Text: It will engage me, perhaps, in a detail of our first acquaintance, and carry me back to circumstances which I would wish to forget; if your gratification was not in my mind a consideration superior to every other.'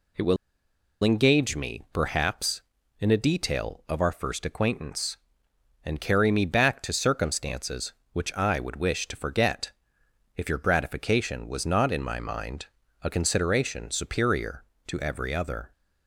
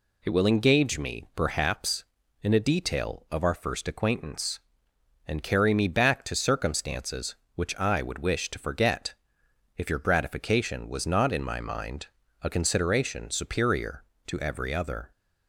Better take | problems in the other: second | pauses between "will" and "engage"; noticeable; at 0.3 s; 0.67 s long // pauses between "mind" and "a"; slight; at 12.6 s; 0.34 s long; slight in the second

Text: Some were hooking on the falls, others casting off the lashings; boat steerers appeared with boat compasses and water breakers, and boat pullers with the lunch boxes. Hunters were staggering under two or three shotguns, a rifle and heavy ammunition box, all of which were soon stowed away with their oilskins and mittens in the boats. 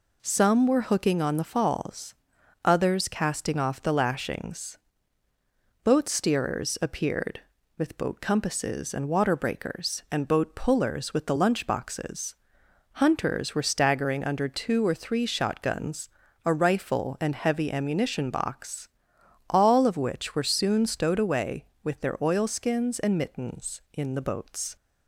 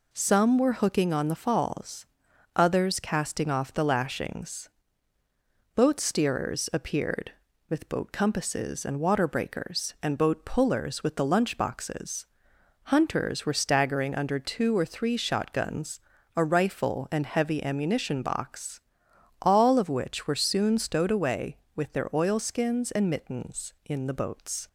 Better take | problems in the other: neither | none

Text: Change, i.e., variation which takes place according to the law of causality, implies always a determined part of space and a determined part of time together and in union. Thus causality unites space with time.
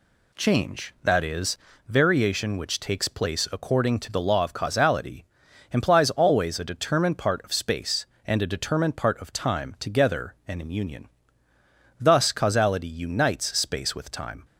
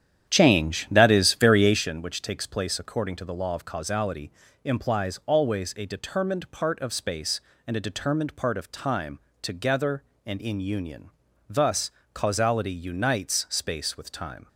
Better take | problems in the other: first | starts louder than the rest; strong; until 1.9 s; 9.5 dB // pauses between "time" and "together"; slight; at 9.1 s; 0.22 s long // pauses between "Thus" and "causality"; slight; at 11.8 s; 0.22 s long

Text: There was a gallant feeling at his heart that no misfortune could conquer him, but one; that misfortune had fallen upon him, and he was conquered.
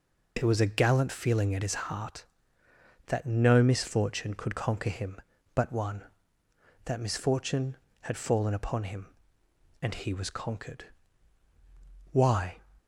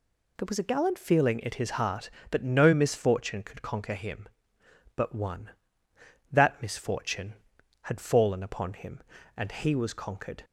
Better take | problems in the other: second | goes on to say "Why"; slight; from 12.1 s on; 0.46 s long

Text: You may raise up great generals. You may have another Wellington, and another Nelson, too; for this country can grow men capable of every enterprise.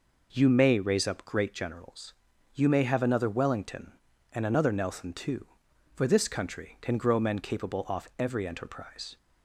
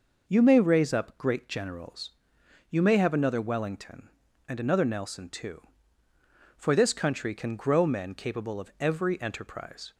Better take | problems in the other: second | says "off" for "of"; at 7.8 s

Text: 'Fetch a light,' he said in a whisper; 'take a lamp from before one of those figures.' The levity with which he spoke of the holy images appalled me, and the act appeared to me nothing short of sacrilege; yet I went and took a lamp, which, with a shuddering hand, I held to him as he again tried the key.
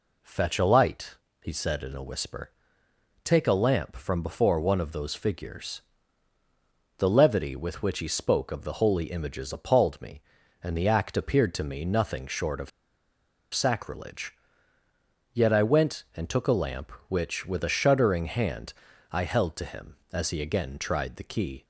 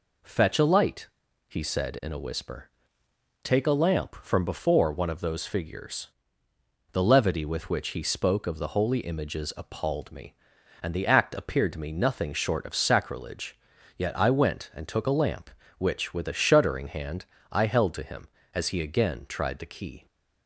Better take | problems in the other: second | pauses between "of" and "sacrilege"; noticeable; at 12.6 s; 0.84 s long

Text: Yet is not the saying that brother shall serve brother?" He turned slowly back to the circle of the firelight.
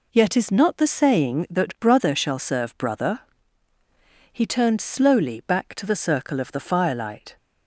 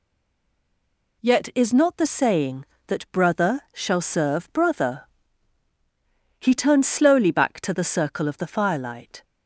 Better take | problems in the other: first | stays silent before the first word; noticeable; until 1.2 s; 1.2 s long

